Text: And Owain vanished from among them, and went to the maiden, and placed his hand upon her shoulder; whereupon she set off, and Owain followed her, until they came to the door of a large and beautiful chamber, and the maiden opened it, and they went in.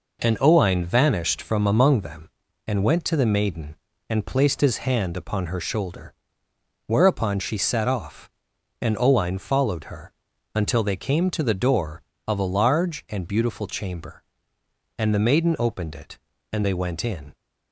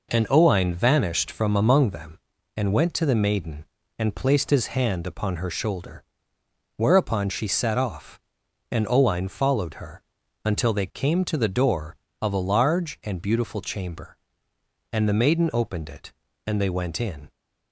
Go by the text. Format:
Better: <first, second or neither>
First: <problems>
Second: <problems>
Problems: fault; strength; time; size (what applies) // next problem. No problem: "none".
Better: neither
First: none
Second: none